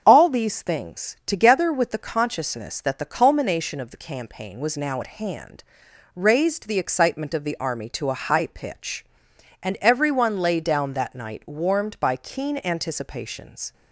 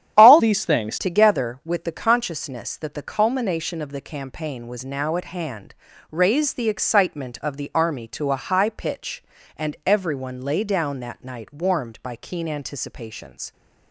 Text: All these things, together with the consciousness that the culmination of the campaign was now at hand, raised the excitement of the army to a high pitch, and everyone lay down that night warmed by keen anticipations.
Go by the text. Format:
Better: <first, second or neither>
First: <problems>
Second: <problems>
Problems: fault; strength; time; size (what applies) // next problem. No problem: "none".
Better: first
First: starts louder than the rest; strong; until 1.0 s; 7 dB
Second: starts louder than the rest; strong; until 1.1 s; 10 dB // changes voice from "these" to "things"; from 0.3 to 0.9 s; 0.6 s long